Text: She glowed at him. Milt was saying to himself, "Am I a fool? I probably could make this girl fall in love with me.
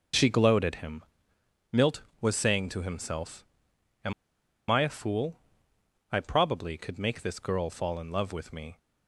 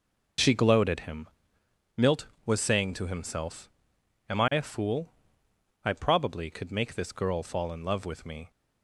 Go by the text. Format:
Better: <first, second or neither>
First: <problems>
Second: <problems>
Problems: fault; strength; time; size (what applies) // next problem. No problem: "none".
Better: second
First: pauses between "Am" and "I"; noticeable; at 4.1 s; 0.56 s long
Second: none